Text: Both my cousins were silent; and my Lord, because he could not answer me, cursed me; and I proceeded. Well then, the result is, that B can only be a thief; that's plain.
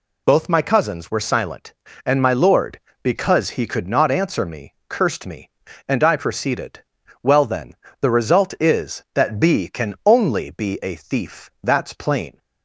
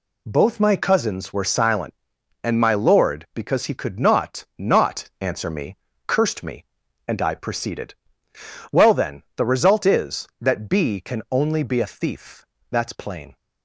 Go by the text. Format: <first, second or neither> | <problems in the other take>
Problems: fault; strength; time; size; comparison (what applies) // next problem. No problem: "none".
first | says "not" twice; at 4.5 s